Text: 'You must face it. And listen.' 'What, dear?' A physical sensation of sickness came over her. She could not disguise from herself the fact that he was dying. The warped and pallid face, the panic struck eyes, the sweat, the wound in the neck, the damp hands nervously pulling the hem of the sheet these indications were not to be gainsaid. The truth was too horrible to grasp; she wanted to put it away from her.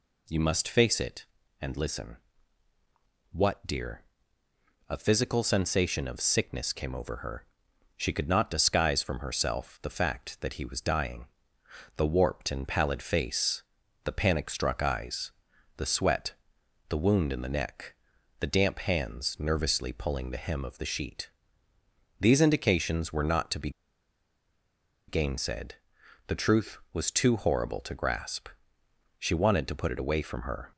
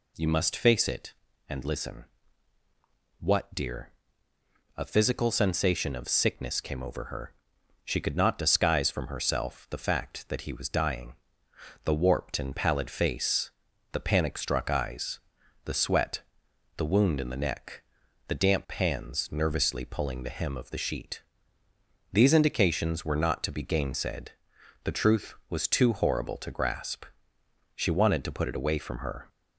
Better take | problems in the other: second | pauses between "sheet" and "these"; noticeable; at 21.2 s; 0.90 s long; noticeable in the second // pauses between "be" and "gainsaid"; strong; at 23.6 s; 1.3 s long

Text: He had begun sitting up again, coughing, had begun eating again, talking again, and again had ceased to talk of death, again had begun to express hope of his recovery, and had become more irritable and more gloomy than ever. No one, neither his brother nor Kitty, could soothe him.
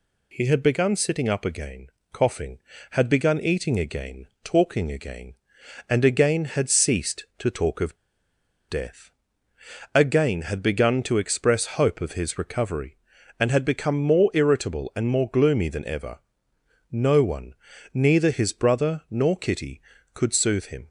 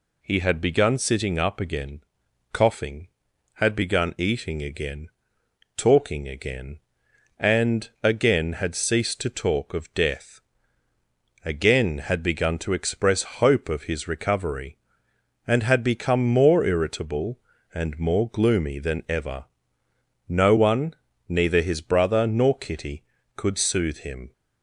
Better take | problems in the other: second | pauses between "of" and "death"; noticeable; at 7.9 s; 0.73 s long

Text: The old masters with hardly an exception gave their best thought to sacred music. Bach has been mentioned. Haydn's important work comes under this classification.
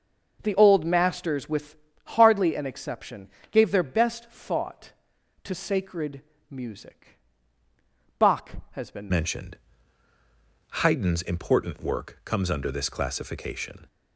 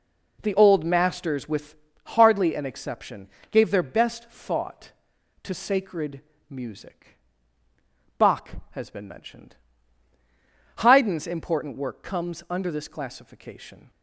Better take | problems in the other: second | pauses between "with" and "hardly"; slight; at 1.7 s; 0.28 s long; slight in the second // pauses between "exception" and "gave"; slight; at 3.2 s; 0.22 s long; slight in the second // pauses between "sacred" and "music"; slight; at 6.2 s; 0.28 s long; slight in the second // changes voice at "mentioned"; from 9.0 s on; 4.8 s long

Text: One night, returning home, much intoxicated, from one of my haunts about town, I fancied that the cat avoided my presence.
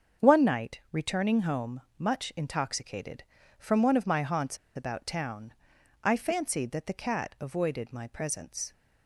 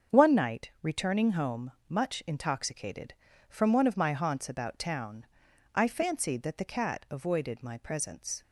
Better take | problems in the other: second | starts louder than the rest; until 1.3 s; 7 dB; also in the second // pauses between "haunts" and "about"; slight; at 4.5 s; 0.18 s long

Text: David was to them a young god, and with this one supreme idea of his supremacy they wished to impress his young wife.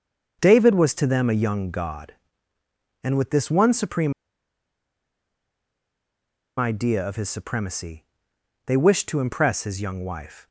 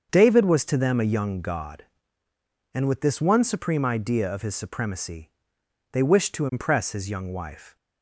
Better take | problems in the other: second | starts louder than the rest; until 1.4 s; 6.5 dB; also in the second // pauses between "supreme" and "idea"; strong; at 4.1 s; 2.4 s long // pauses between "supremacy" and "they"; noticeable; at 8.0 s; 0.62 s long; noticeable in the second

